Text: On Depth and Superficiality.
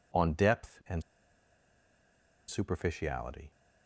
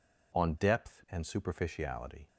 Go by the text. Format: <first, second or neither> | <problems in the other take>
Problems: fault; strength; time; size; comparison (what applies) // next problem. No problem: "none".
second | pauses between "and" and "Superficiality"; strong; at 1.0 s; 1.4 s long